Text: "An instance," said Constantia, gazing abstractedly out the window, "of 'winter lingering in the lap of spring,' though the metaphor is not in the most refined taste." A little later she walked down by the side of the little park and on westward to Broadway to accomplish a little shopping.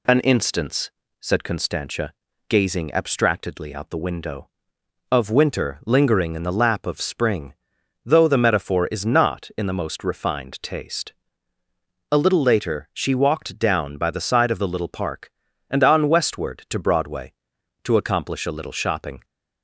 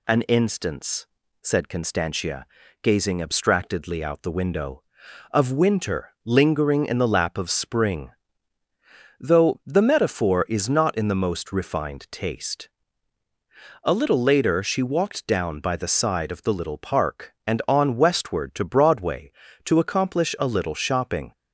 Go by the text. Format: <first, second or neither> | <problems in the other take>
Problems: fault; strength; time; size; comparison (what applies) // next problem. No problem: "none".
neither | none